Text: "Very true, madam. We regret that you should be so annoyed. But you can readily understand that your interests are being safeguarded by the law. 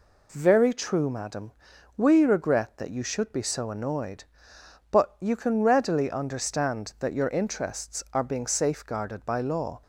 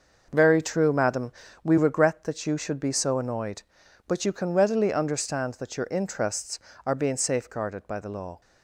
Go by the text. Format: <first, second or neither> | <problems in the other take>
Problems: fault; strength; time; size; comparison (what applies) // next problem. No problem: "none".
second | skips "the"; at 9.4 s